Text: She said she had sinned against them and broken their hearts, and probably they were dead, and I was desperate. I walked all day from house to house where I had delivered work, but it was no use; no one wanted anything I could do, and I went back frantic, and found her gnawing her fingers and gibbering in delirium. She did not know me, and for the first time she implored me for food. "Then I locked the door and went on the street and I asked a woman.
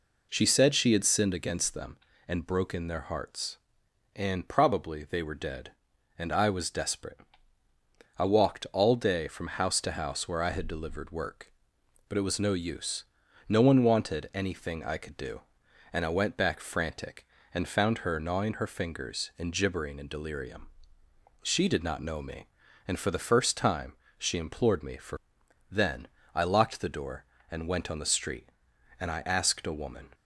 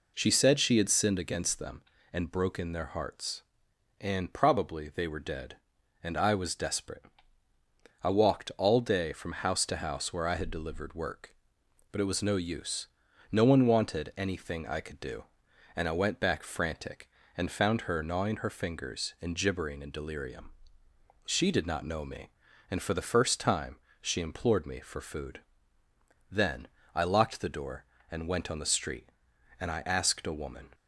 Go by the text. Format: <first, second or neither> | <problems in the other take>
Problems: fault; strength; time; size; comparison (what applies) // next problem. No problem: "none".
second | pauses between "time" and "she"; slight; at 23.9 s; 0.22 s long; slight in the second // skips "food"; at 25.4 s // pauses between "Then" and "I"; slight; at 26.0 s; 0.26 s long; slight in the second